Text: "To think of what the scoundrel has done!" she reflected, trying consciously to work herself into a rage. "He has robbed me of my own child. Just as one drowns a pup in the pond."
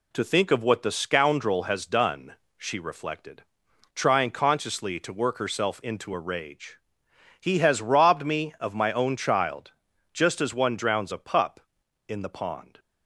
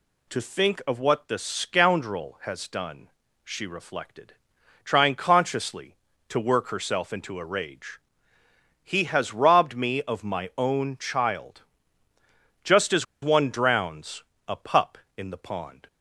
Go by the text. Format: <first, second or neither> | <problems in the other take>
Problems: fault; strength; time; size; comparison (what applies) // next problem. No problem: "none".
first | pauses between "as" and "one"; slight; at 13.0 s; 0.17 s long // pauses between "drowns" and "a"; slight; at 14.2 s; 0.24 s long